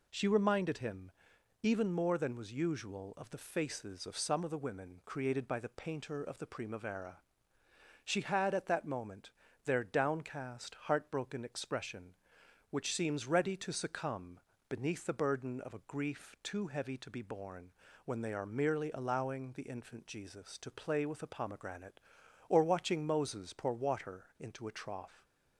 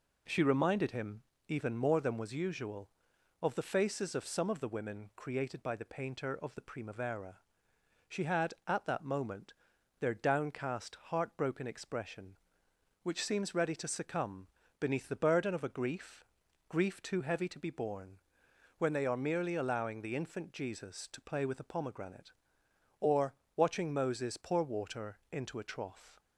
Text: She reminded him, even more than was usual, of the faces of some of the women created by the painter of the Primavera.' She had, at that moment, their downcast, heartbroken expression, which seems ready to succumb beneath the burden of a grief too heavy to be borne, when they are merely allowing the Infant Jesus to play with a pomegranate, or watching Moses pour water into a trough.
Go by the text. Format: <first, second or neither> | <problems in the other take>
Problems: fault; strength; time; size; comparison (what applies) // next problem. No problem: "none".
first | pauses between "succumb" and "beneath"; slight; at 14.4 s; 0.32 s long; slight in the first // says "grief" twice; at 16.6 s // pauses between "or" and "watching"; slight; at 23.3 s; 0.22 s long